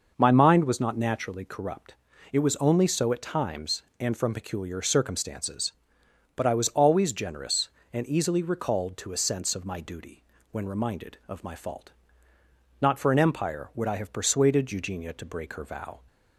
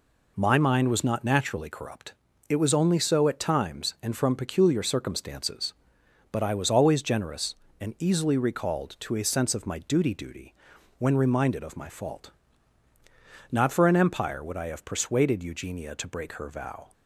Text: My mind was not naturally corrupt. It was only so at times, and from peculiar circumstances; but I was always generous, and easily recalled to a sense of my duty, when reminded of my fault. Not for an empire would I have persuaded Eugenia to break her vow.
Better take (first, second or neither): first